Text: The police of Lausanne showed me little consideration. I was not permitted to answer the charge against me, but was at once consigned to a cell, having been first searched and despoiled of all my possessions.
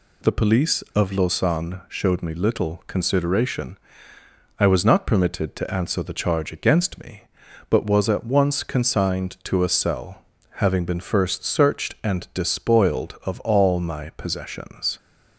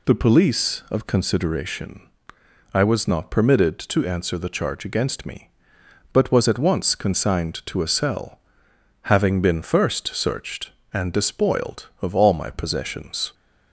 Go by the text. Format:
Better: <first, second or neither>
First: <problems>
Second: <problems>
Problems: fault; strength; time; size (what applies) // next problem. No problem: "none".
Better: first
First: none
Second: skips "Lausanne showed me little"; at 1.0 s